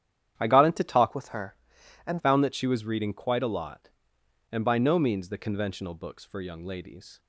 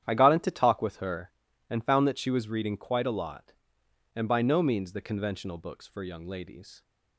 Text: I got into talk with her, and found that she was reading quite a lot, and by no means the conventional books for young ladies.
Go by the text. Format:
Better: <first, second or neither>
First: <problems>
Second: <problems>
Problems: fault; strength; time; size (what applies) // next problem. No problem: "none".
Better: second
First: starts louder than the rest; strong; until 1.3 s; 10 dB // changes voice from "with" to "and"; from 1.1 to 2.2 s; 1.1 s long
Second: starts louder than the rest; strong; until 1.0 s; 10 dB